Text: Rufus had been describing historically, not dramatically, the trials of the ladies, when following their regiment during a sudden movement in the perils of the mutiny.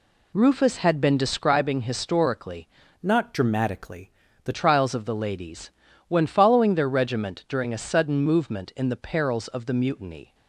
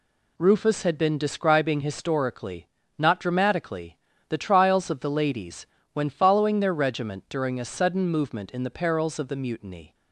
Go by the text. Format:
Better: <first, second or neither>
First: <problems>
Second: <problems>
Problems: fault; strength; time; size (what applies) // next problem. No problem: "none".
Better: second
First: changes voice from "not" to "the"; from 3.0 to 4.5 s; 1.5 s long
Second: none